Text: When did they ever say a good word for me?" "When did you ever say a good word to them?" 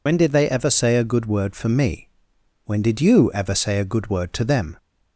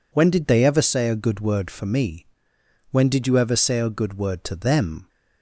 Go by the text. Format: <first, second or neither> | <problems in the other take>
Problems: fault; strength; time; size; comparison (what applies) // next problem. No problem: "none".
second | loses the start of "When"; at 0.0 s; 55 ms